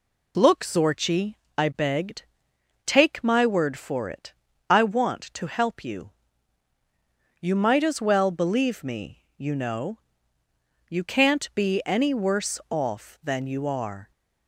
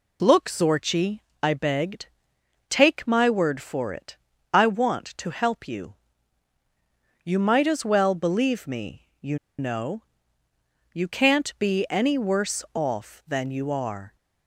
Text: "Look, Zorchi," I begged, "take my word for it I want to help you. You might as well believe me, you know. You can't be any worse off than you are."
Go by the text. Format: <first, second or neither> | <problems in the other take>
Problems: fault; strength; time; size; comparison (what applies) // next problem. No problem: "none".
first | pauses between "it" and "I"; slight; at 4.1 s; 0.36 s long; slight in the first // pauses between "you" and "know"; slight; at 9.3 s; 0.21 s long